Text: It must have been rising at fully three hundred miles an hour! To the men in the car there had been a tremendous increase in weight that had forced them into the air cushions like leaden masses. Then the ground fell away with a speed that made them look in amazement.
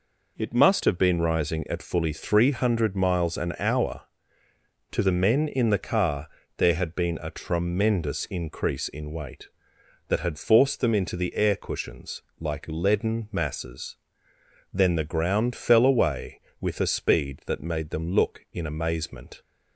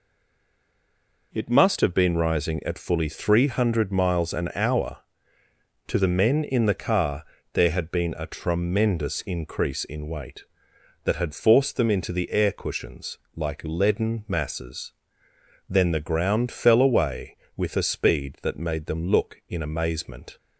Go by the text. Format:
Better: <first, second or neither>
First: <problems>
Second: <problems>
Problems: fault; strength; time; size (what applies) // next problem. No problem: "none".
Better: first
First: pauses between "car" and "there"; slight; at 6.2 s; 0.28 s long // pauses between "cushions" and "like"; slight; at 12.2 s; 0.18 s long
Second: stays silent before the first word; noticeable; until 1.3 s; 1.3 s long // pauses between "car" and "there"; slight; at 7.2 s; 0.28 s long // pauses between "cushions" and "like"; slight; at 13.1 s; 0.18 s long